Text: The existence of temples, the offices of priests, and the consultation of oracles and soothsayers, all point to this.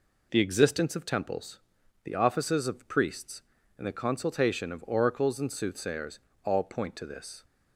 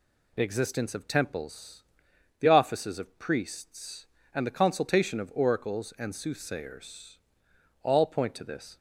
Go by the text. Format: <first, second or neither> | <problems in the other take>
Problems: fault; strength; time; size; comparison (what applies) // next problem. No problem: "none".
neither | none